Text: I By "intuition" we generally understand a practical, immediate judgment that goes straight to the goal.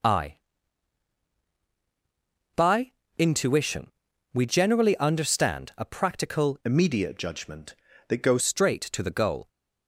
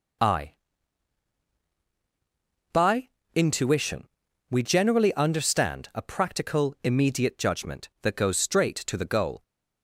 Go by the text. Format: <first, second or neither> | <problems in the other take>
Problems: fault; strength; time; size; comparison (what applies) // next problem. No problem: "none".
second | pauses between "By" and "intuition"; slight; at 2.9 s; 0.24 s long; slight in the second // pauses between "intuition" and "we"; at 3.8 s; 0.44 s long; also in the second // changes voice from "immediate" to "goes"; from 6.6 to 8.4 s; 1.8 s long